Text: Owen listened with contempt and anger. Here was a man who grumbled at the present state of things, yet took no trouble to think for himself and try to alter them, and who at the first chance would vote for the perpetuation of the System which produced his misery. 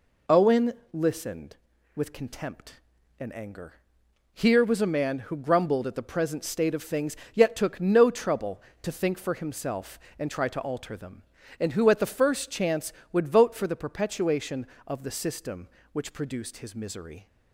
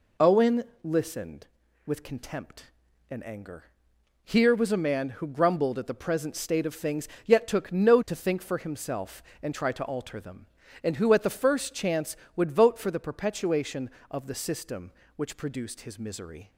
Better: first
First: pauses between "Owen" and "listened"; slight; at 0.7 s; 0.22 s long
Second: pauses between "Owen" and "listened"; slight; at 0.6 s; 0.22 s long // skips "trouble"; at 8.0 s

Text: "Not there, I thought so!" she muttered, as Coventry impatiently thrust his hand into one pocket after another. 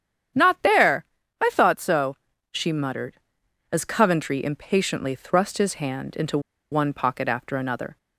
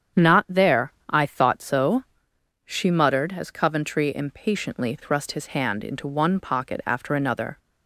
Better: second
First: starts louder than the rest; strong; until 1.7 s; 9 dB // pauses between "into" and "one"; slight; at 6.3 s; 0.32 s long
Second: starts louder than the rest; strong; until 1.3 s; 8 dB

